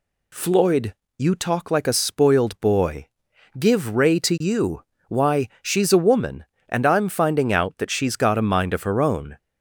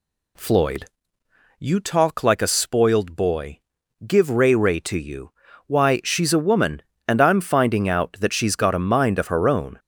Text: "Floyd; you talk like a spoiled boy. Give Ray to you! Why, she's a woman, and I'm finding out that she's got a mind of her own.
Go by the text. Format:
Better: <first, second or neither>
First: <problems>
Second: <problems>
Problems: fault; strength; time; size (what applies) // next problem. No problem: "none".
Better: first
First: none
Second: says "Ray" twice; at 4.5 s